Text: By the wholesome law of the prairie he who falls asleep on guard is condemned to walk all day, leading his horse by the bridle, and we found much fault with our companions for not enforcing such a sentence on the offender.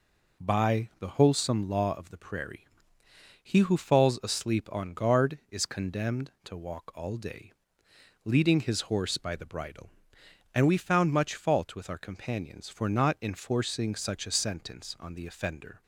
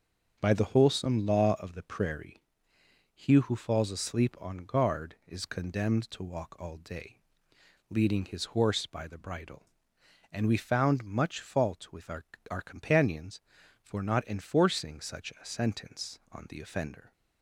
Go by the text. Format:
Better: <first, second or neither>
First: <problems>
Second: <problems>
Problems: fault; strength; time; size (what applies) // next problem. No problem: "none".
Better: first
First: pauses between "prairie" and "he"; noticeable; at 2.6 s; 0.74 s long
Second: starts louder than the rest; until 1.4 s; 6.5 dB // pauses between "prairie" and "he"; noticeable; at 2.4 s; 0.72 s long // says "our" twice; at 12.5 s